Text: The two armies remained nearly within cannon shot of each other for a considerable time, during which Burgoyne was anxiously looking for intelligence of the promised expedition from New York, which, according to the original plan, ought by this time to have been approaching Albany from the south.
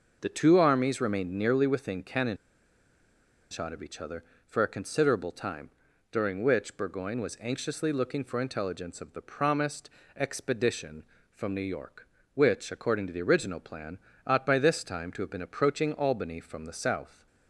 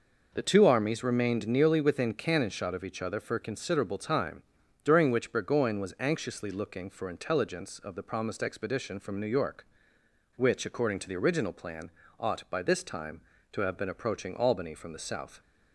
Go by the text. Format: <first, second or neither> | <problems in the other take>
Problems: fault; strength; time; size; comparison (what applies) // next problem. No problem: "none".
second | pauses between "cannon" and "shot"; at 2.3 s; 1.1 s long // pauses between "promised" and "expedition"; slight; at 9.9 s; 0.26 s long